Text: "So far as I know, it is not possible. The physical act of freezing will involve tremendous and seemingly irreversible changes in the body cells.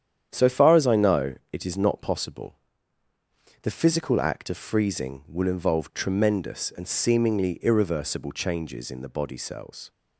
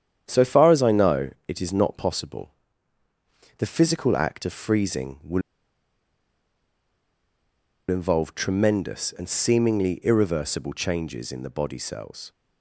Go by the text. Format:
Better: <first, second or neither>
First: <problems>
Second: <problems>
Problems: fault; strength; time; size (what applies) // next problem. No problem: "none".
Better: first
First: starts louder than the rest; strong; until 1.3 s; 9 dB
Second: starts louder than the rest; strong; until 1.2 s; 9 dB // pauses between "will" and "involve"; strong; at 5.4 s; 2.4 s long